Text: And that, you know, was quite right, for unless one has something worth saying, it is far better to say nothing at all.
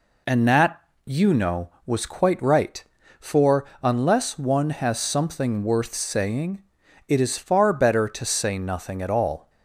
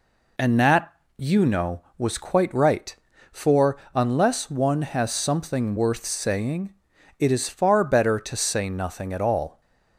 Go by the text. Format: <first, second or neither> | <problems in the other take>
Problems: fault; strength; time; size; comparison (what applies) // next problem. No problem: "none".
neither | pauses between "for" and "unless"; slight; the same in both